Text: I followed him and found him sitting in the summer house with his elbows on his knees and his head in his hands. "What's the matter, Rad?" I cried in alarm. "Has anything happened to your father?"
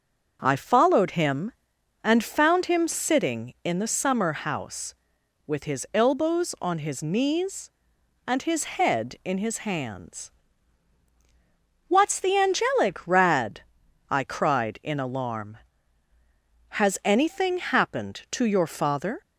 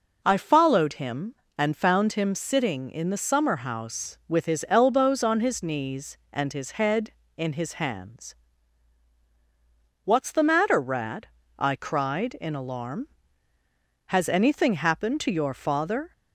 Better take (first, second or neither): second